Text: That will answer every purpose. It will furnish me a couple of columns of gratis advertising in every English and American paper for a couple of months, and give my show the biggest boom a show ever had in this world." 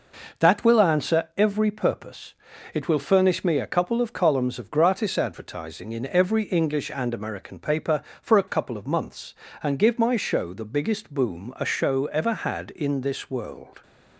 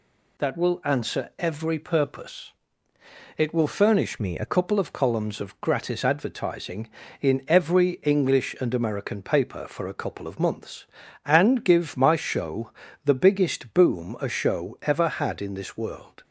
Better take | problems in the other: first | changes voice from "me" to "a"; from 4.1 to 4.4 s; 0.3 s long // pauses between "show" and "the"; slight; at 12.7 s; 0.34 s long

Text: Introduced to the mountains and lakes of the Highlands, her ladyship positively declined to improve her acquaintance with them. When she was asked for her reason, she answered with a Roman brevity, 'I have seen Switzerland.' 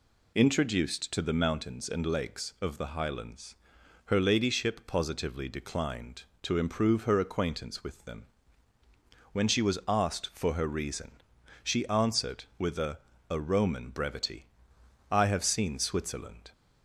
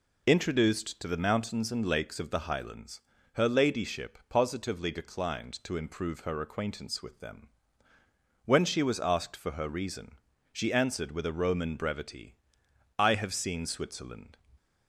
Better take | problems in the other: second | says "a" twice; at 13.2 s

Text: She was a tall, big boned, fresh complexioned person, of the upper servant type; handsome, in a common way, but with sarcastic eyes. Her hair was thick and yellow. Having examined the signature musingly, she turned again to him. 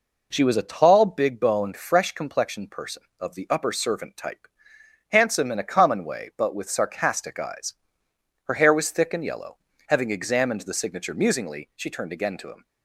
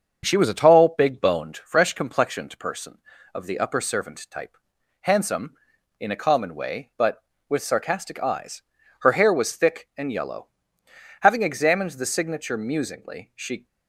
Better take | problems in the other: first | starts louder than the rest; until 1.2 s; 7 dB // stops before "turned again to him"; at 13.6 s

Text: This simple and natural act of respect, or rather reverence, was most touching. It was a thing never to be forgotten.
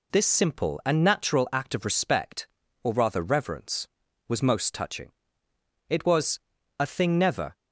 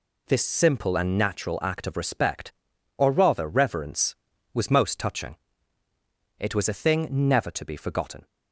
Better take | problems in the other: second | pauses between "was" and "a"; at 6.3 s; 0.40 s long // stops before "to be forgotten"; at 7.5 s

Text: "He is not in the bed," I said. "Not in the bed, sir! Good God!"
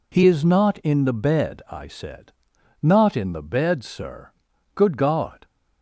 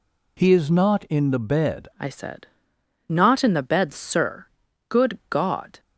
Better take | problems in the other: first | changes voice at "I"; from 1.9 s on; 3.8 s long

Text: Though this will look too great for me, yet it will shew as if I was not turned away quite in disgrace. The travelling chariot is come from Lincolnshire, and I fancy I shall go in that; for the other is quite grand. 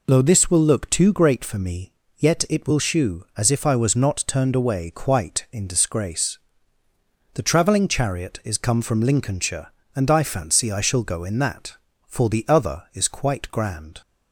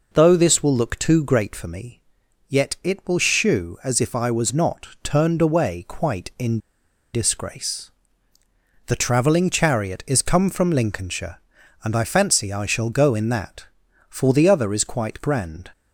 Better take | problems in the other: first | pauses between "not" and "turned"; slight; at 4.8 s; 0.16 s long // pauses between "in" and "disgrace"; noticeable; at 6.5 s; 0.56 s long

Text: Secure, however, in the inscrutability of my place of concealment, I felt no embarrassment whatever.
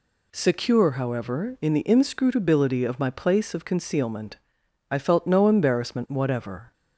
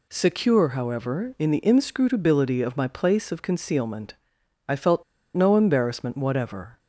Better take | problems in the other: first | pauses between "felt" and "no"; slight; at 5.0 s; 0.31 s long

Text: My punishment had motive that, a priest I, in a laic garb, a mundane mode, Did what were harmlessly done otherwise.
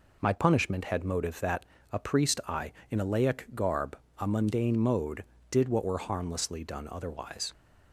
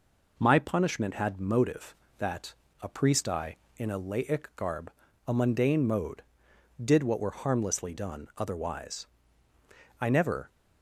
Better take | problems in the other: first | goes on to say "I never"; slight; from 10.0 s on; 0.48 s long

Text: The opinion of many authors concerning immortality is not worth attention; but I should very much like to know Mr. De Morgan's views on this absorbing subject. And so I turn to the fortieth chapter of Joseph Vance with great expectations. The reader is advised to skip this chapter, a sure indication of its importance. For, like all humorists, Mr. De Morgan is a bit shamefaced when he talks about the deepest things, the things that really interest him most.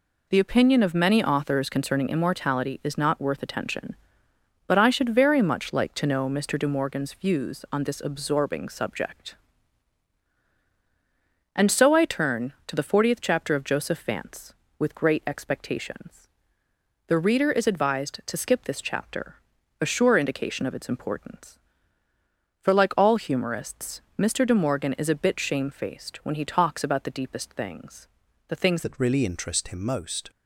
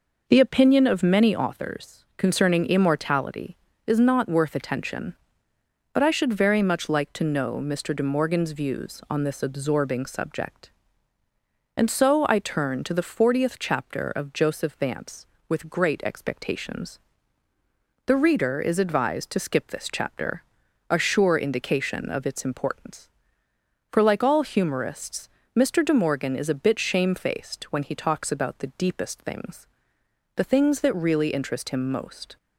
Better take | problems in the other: second | changes voice at "that"; from 28.8 s on; 1.4 s long

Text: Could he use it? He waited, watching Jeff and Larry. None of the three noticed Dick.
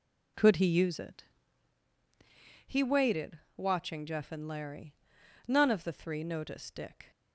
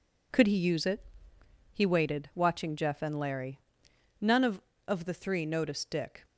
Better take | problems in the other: first | says "of" twice; at 4.8 s

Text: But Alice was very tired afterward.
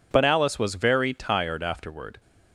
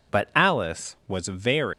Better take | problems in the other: first | stops before "tired afterward"; at 1.7 s

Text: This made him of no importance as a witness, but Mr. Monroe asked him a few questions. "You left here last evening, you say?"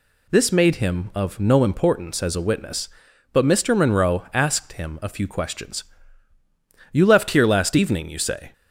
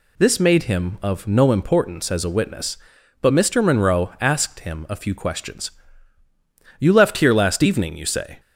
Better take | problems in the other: neither | none

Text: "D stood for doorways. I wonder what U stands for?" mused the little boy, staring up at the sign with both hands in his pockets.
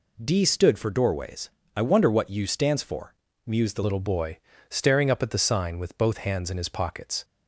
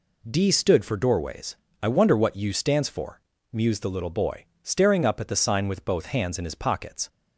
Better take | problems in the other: second | changes voice at "little"; from 3.8 s on; 3.4 s long

